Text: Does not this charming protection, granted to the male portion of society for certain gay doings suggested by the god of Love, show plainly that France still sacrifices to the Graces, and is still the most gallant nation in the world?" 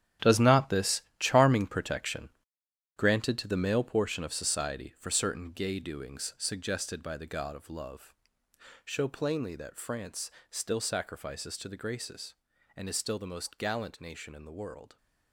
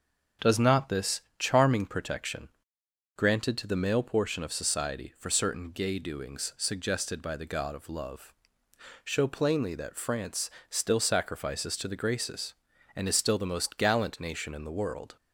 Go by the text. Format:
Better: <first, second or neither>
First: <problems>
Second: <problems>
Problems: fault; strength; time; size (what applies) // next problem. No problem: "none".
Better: second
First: gets quieter; strong; throughout; 12.5 dB // starts louder than the rest; strong; until 1.3 s; 11 dB // pauses between "this" and "charming"; slight; at 1.0 s; 0.18 s long // pauses between "France" and "still"; slight; at 10.3 s; 0.20 s long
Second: starts louder than the rest; strong; until 1.5 s; 7.5 dB // pauses between "this" and "charming"; slight; at 1.1 s; 0.18 s long // pauses between "France" and "still"; slight; at 10.4 s; 0.20 s long